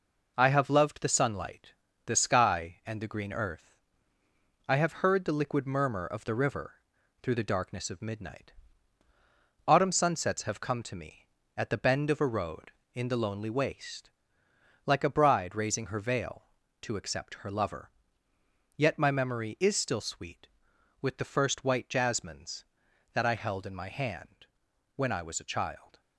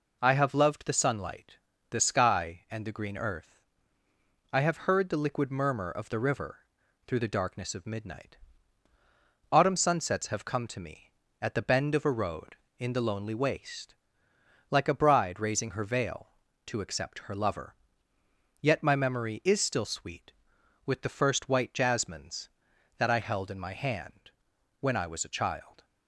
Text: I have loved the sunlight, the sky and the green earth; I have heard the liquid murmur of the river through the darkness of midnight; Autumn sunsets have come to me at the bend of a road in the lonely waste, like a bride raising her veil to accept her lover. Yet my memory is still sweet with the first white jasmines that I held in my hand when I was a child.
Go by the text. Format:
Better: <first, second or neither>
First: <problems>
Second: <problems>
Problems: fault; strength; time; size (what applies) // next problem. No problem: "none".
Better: second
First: gets quieter; noticeable; throughout; 5.5 dB // pauses between "river" and "through"; noticeable; at 6.7 s; 0.50 s long // pauses between "hand" and "when"; noticeable; at 24.4 s; 0.50 s long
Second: pauses between "river" and "through"; noticeable; at 6.5 s; 0.50 s long // pauses between "hand" and "when"; noticeable; at 24.3 s; 0.50 s long